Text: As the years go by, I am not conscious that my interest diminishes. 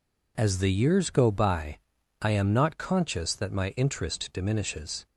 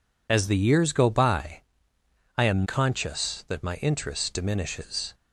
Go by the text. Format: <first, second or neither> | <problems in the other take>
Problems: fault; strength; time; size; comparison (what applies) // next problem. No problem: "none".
first | skips "not"; at 2.6 s